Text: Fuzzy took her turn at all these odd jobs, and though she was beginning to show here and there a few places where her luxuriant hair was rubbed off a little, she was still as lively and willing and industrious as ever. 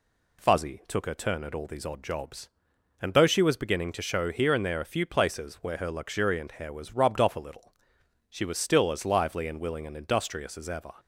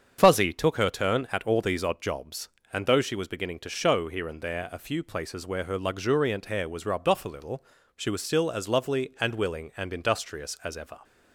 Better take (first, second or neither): first